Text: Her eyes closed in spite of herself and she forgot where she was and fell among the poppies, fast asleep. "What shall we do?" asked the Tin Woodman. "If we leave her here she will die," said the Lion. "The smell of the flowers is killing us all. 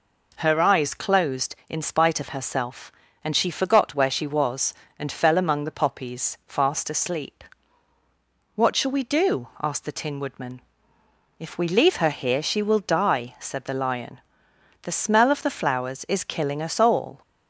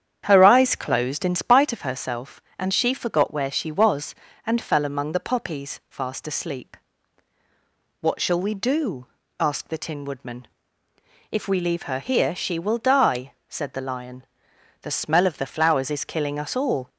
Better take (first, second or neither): first